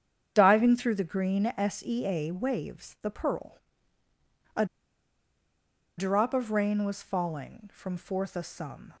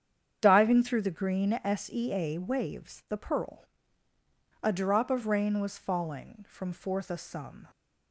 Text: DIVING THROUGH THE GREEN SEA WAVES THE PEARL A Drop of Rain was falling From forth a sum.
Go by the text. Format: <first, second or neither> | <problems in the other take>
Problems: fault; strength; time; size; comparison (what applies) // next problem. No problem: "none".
second | starts louder than the rest; strong; until 1.3 s; 8 dB; strong in the second // pauses between "PEARL" and "A"; noticeable; at 3.5 s; 0.96 s long; noticeable in the second // pauses between "A" and "Drop"; strong; at 4.6 s; 1.3 s long